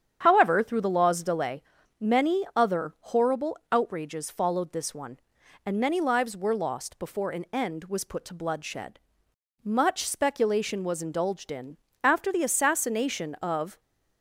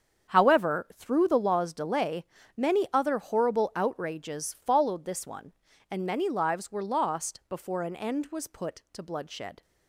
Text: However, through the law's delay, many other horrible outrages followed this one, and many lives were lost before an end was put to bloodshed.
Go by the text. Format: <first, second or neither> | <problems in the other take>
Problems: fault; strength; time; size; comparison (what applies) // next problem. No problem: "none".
second | starts louder than the rest; strong; until 1.2 s; 9 dB; strong in the second // goes on to say "Much speculation was indulged in after the assassination of"; strong; from 9.6 s on; 4.1 s long